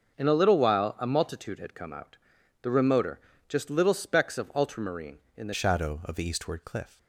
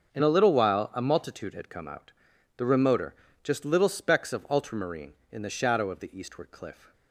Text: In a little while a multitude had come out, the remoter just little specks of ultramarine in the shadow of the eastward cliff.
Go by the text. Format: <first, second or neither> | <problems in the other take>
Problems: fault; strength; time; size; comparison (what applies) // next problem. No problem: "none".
second | starts louder than the rest; until 1.2 s; 6.5 dB; also in the second // pauses between "remoter" and "just"; slight; at 3.1 s; 0.28 s long; slight in the second // changes voice at "shadow"; from 5.5 s on; 1.4 s long